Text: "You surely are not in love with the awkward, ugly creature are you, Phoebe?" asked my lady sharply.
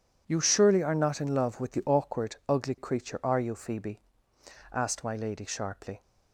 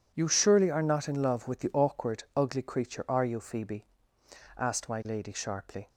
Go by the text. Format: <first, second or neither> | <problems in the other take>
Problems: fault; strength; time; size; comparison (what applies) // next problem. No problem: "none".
neither | none